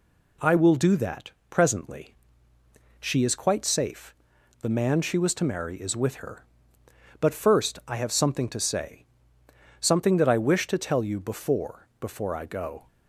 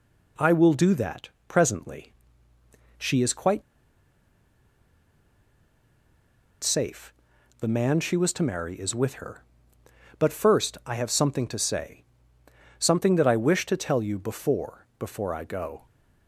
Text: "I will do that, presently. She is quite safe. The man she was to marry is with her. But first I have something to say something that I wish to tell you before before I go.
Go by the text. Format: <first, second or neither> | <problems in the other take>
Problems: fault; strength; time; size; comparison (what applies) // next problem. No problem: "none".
first | pauses between "quite" and "safe"; strong; at 3.6 s; 3.0 s long // pauses between "say" and "something"; noticeable; at 12.0 s; 0.74 s long; noticeable in the first